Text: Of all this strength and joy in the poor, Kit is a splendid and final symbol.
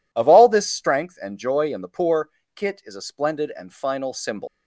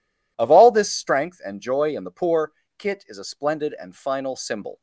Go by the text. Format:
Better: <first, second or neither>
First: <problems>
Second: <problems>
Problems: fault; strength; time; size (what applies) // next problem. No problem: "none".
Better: second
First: leaves "symbol" unfinished; at 4.4 s; 100 ms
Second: none